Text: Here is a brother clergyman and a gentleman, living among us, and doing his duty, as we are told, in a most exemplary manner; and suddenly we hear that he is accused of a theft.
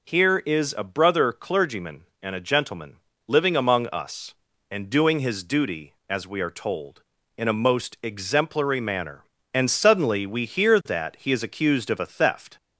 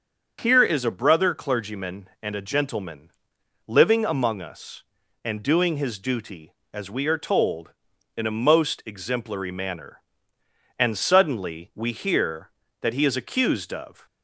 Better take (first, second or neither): first